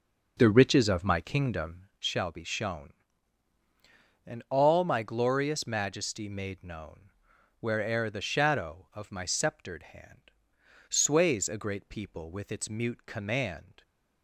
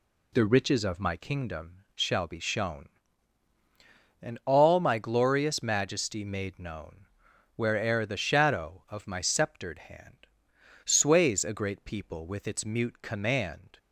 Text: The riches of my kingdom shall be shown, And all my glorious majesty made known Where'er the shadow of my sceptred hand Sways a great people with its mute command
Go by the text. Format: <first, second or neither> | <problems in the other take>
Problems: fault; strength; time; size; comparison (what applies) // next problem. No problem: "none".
second | starts louder than the rest; noticeable; until 1.9 s; 6 dB // pauses between "known" and "Where'er"; noticeable; at 7.0 s; 0.48 s long; noticeable in the second // pauses between "hand" and "Sways"; noticeable; at 10.2 s; 0.58 s long; noticeable in the second